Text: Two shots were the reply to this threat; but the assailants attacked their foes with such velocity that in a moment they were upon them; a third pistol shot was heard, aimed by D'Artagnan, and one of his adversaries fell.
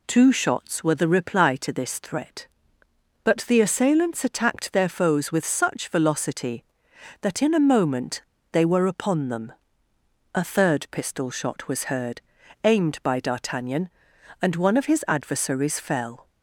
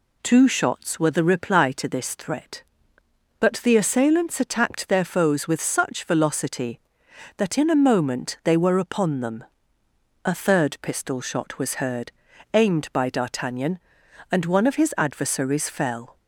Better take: second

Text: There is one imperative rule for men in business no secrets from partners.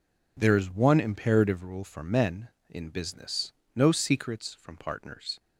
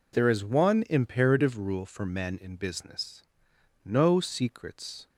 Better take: first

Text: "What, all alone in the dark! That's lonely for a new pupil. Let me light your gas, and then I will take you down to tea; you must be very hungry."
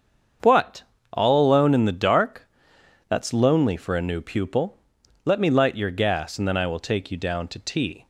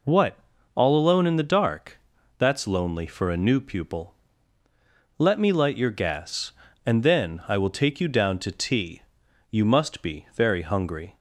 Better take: second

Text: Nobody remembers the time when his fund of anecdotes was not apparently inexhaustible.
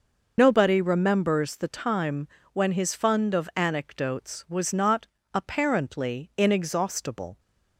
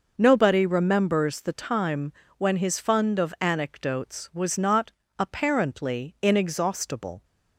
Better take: second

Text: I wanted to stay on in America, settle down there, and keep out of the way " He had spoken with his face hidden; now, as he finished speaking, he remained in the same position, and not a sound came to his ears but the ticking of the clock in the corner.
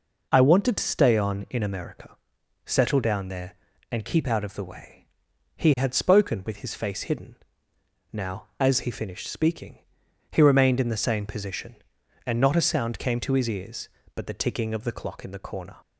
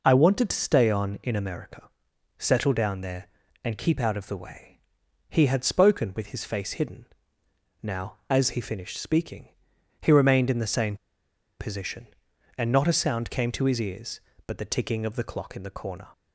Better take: first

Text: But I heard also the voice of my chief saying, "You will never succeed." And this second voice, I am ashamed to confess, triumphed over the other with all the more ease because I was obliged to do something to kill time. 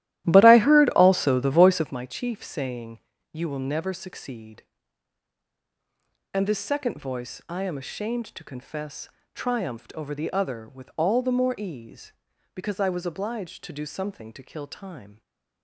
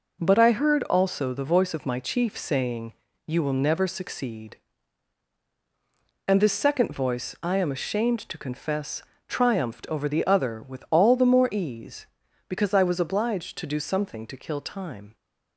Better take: second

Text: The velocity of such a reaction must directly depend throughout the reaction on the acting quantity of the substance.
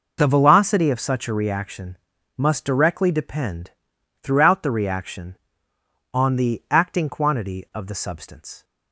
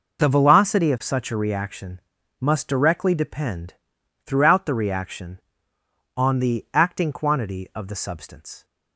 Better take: neither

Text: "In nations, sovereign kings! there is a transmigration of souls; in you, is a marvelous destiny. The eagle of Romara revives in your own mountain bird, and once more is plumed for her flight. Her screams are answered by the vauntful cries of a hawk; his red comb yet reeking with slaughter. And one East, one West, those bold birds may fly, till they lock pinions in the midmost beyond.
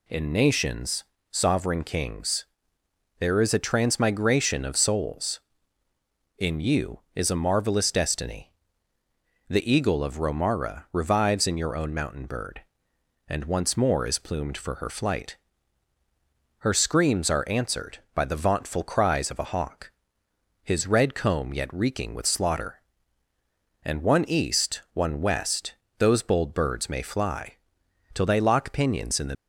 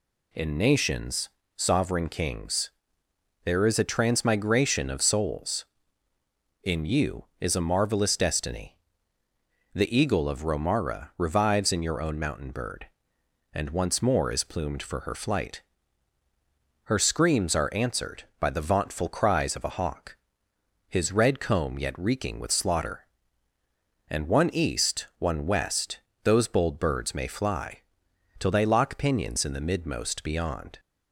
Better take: second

